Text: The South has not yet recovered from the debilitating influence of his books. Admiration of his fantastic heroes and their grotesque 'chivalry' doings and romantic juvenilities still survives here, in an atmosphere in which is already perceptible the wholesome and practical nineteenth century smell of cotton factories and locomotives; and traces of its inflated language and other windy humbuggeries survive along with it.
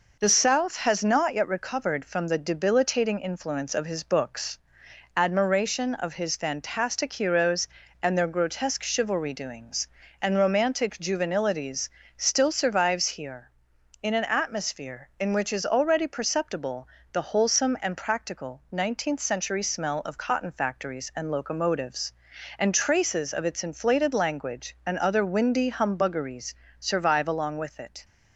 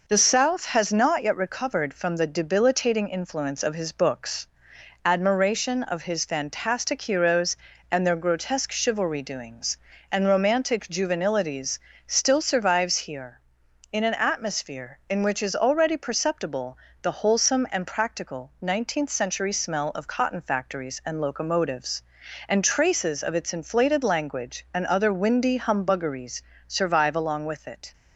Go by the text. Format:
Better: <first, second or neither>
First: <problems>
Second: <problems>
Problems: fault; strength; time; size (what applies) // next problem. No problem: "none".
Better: neither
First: pauses between "juvenilities" and "still"; slight; at 11.8 s; 0.26 s long // pauses between "perceptible" and "the"; slight; at 16.8 s; 0.26 s long // pauses between "humbuggeries" and "survive"; slight; at 26.5 s; 0.26 s long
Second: pauses between "juvenilities" and "still"; slight; at 11.7 s; 0.26 s long // pauses between "perceptible" and "the"; slight; at 16.7 s; 0.26 s long // pauses between "humbuggeries" and "survive"; slight; at 26.4 s; 0.26 s long